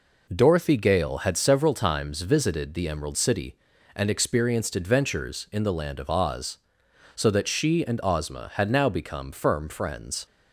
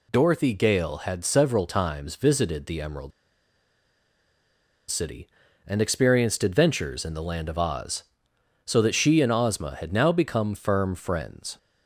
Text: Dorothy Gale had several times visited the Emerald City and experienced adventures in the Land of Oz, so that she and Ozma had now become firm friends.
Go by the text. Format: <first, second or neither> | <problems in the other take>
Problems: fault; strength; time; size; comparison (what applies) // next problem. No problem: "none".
first | pauses between "Emerald" and "City"; strong; at 3.1 s; 1.8 s long